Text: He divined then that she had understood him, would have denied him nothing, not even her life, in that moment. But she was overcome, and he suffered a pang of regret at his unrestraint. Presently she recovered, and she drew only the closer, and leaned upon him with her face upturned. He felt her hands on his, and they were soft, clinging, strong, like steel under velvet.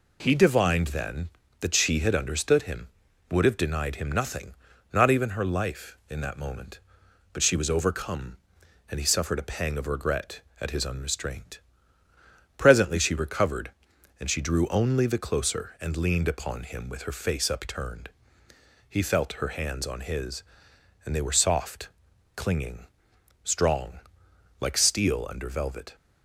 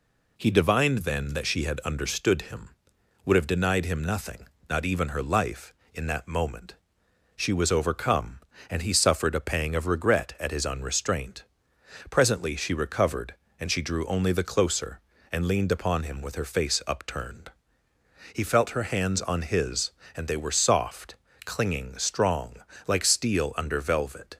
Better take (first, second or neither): first